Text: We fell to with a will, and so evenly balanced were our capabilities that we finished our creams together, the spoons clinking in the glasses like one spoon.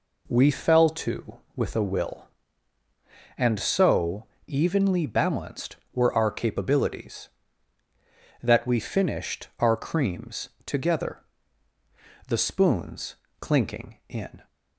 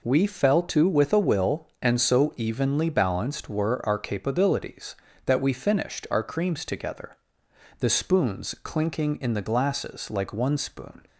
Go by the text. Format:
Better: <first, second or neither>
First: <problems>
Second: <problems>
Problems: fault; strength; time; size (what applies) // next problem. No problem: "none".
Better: second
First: pauses between "so" and "evenly"; slight; at 4.2 s; 0.24 s long // pauses between "creams" and "together"; slight; at 10.4 s; 0.16 s long // pauses between "spoons" and "clinking"; slight; at 13.1 s; 0.24 s long // stops before "the glasses like one spoon"; at 14.4 s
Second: none